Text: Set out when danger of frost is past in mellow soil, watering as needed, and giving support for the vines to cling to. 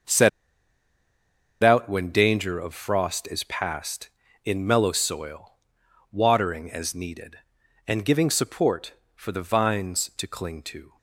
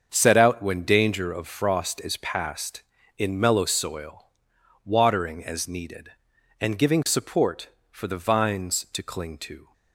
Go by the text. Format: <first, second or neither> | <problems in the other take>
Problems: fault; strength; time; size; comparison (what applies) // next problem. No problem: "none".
second | starts louder than the rest; until 2.4 s; 6.5 dB; also in the second // pauses between "Set" and "out"; strong; at 0.2 s; 1.3 s long